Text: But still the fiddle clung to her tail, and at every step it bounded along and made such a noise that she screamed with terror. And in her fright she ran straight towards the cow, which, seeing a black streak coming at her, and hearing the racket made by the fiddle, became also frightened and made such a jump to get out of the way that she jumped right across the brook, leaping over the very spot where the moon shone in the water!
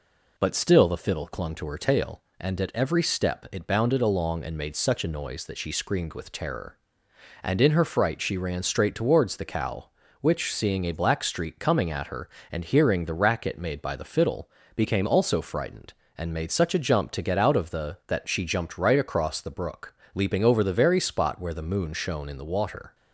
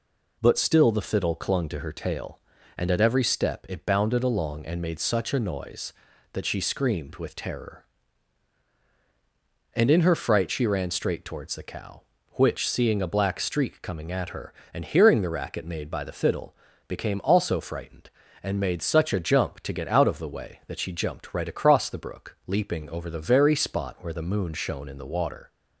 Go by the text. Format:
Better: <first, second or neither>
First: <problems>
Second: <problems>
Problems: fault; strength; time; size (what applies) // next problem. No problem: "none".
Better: second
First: skips "way"; at 18.0 s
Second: none